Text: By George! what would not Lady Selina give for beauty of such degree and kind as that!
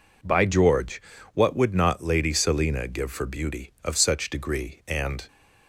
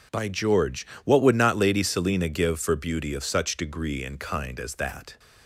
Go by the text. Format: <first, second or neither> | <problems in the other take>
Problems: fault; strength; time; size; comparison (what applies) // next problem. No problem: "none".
second | stops before "kind as that"; at 5.2 s